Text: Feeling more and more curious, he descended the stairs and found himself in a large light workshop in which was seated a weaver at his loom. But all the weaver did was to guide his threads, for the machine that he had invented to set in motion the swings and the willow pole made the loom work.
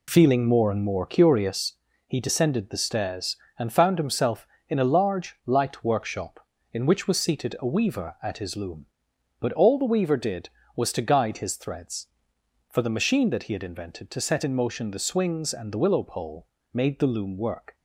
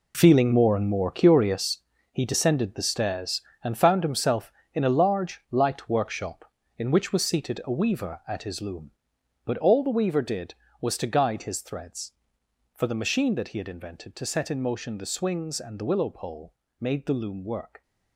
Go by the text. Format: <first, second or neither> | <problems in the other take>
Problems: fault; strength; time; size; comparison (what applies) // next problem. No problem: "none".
first | gets quieter; strong; throughout; 12 dB // pauses between "pole" and "made"; slight; at 16.5 s; 0.26 s long; slight in the first